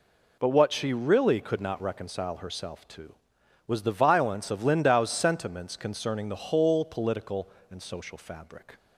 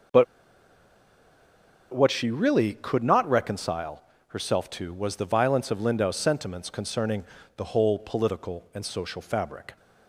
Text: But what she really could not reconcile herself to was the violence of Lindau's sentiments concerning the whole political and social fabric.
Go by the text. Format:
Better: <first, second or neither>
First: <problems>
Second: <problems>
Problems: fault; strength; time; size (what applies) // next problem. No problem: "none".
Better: first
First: none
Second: pauses between "But" and "what"; strong; at 0.2 s; 1.6 s long // pauses between "reconcile" and "herself"; slight; at 4.0 s; 0.26 s long // pauses between "concerning" and "the"; slight; at 7.2 s; 0.34 s long